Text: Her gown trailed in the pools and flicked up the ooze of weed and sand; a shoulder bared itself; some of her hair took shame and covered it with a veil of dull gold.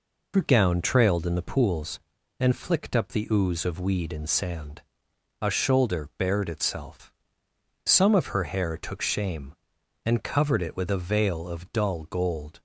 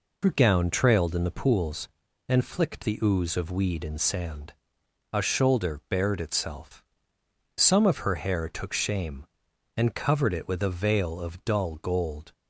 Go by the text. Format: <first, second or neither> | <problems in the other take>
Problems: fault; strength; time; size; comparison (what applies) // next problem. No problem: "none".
first | skips "up"; at 2.8 s